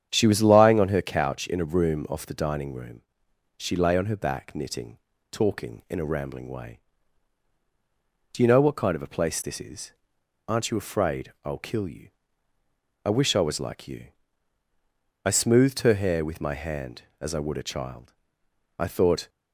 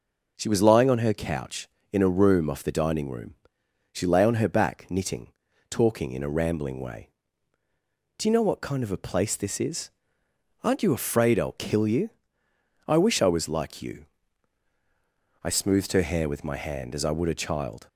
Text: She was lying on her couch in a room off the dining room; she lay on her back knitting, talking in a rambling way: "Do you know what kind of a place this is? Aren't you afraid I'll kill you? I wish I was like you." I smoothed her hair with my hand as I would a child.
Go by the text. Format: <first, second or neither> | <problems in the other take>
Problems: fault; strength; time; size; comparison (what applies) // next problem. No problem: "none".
second | starts louder than the rest; strong; until 1.1 s; 9 dB // goes on to say "I thought"; from 18.7 s on; 0.50 s long